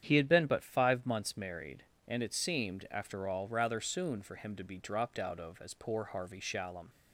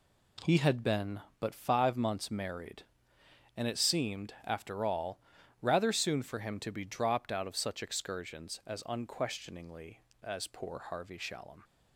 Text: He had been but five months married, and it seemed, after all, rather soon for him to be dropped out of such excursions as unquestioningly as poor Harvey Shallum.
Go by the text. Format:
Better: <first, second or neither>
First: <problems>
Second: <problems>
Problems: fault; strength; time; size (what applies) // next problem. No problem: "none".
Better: second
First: starts louder than the rest; strong; until 1.0 s; 9 dB // skips "such excursions as unquestioningly"; at 5.6 s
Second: none